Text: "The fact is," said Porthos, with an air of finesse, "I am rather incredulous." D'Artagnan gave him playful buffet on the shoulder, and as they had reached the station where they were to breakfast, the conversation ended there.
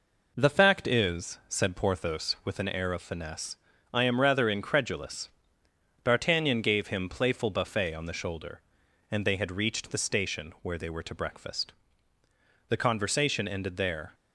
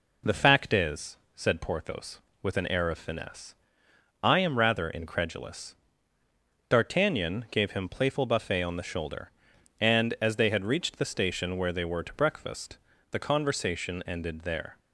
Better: second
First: skips "as"; at 9.2 s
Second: none

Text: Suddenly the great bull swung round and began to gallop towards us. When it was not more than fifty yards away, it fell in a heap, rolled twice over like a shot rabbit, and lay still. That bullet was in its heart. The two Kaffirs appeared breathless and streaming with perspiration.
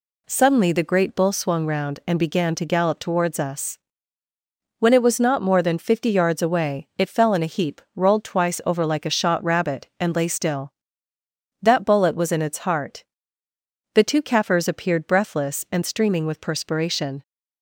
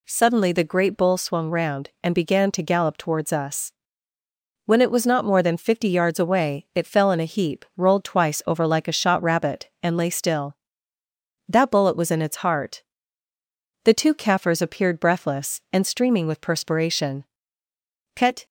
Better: first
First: none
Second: goes on to say "Cut"; slight; from 18.1 s on; 0.30 s long

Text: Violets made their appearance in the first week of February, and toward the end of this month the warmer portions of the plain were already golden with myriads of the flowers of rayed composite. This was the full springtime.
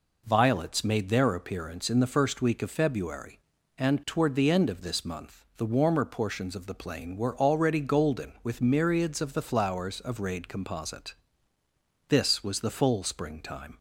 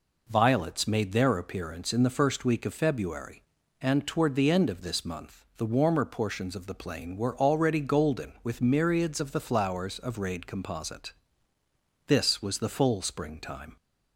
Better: neither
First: none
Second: none

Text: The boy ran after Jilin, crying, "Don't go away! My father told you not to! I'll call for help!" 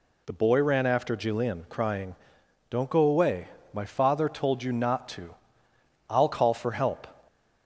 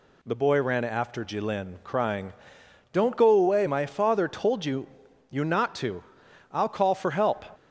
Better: first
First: none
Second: says "you" twice; at 5.3 s

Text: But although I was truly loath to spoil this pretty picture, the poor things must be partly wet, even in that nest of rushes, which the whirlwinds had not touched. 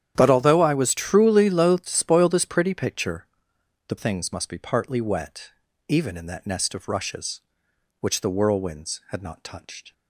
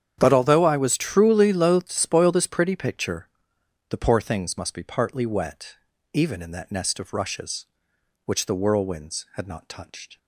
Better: second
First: starts louder than the rest; strong; until 1.1 s; 10 dB // skips "poor"; at 3.9 s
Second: starts louder than the rest; strong; until 1.2 s; 9 dB

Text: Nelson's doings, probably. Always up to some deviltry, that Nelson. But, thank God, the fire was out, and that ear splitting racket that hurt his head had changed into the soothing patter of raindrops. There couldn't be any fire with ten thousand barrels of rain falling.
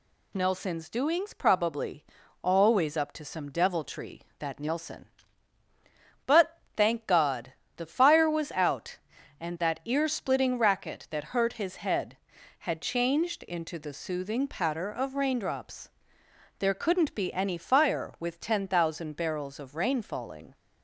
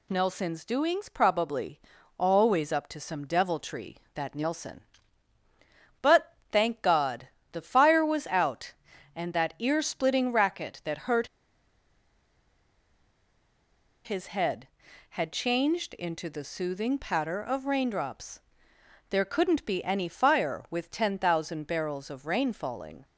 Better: first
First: none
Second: pauses between "hurt" and "his"; strong; at 11.2 s; 2.7 s long

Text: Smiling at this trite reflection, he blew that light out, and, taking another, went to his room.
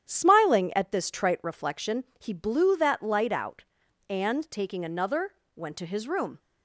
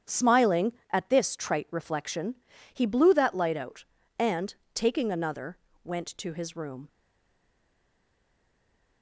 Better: first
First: starts louder than the rest; strong; until 1.1 s; 9.5 dB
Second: starts louder than the rest; strong; until 1.2 s; 8.5 dB // stays silent after the last word; from 6.8 s on; 2.2 s long

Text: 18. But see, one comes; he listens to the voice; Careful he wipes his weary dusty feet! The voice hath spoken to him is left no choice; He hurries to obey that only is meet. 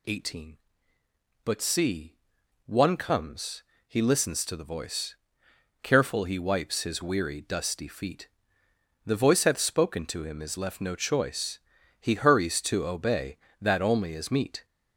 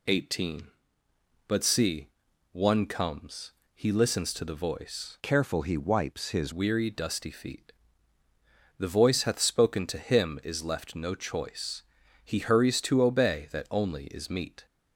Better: first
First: none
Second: changes voice from "Careful" to "his"; from 5.2 to 6.5 s; 1.3 s long

